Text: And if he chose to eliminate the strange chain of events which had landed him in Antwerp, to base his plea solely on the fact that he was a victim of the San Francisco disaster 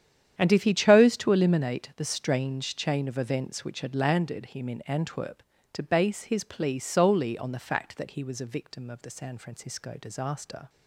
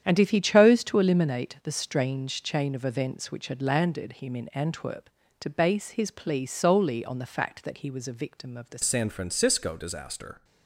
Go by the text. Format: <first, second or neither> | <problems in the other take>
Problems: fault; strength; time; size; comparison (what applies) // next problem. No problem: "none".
first | starts louder than the rest; strong; until 1.0 s; 9.5 dB; strong in the first // changes voice at "San"; from 8.8 s on; 1.6 s long